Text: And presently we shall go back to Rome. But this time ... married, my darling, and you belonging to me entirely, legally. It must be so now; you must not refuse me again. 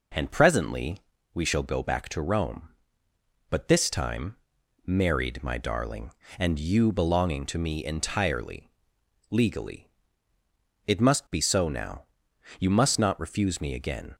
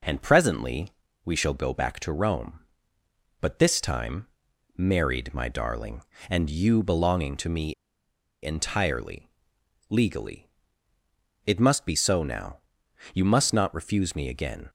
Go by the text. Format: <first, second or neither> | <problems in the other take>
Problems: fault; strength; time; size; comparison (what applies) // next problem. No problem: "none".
first | pauses between "presently" and "we"; slight; at 0.8 s; 0.34 s long; slight in the first // pauses between "me" and "entirely"; noticeable; at 7.7 s; 0.70 s long